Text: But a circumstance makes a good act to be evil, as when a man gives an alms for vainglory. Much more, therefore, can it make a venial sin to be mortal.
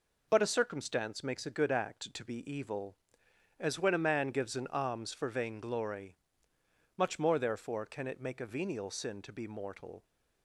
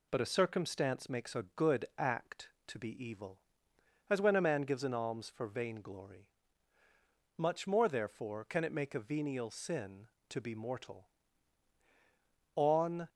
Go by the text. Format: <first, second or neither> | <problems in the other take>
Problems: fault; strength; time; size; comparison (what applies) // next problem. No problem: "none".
first | goes on to say "On"; from 12.5 s on; 0.54 s long